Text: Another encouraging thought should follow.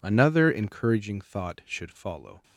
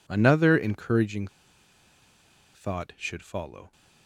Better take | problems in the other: first | pauses between "encouraging" and "thought"; strong; at 1.2 s; 1.2 s long

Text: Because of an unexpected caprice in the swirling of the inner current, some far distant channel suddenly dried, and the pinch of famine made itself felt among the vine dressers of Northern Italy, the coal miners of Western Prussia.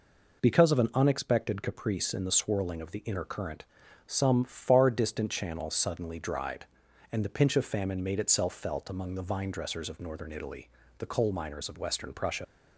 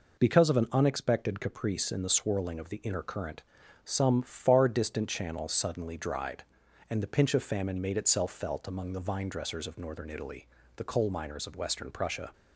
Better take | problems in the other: second | leaves "Prussia" unfinished; at 12.4 s; 95 ms

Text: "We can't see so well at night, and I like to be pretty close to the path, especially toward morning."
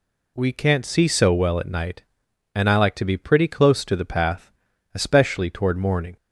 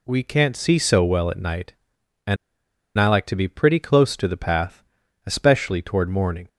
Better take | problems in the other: first | pauses between "and" and "I"; noticeable; at 2.3 s; 0.61 s long

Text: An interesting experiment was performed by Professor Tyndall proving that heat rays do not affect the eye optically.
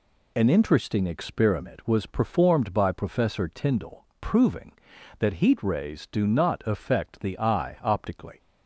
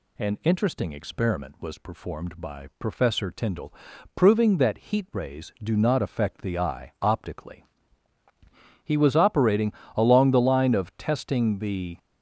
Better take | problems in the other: first | pauses between "Tyndall" and "proving"; at 3.7 s; 0.40 s long; slight in the first // goes on to say "He was operating along the line of testing the"; strong; from 8.8 s on; 3.1 s long

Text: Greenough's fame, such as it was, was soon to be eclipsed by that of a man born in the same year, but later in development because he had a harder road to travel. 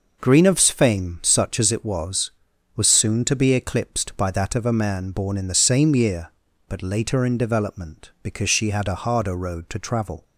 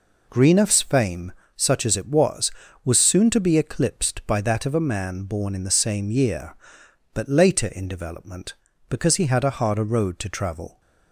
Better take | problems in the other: second | says "she" for "he"; at 8.5 s

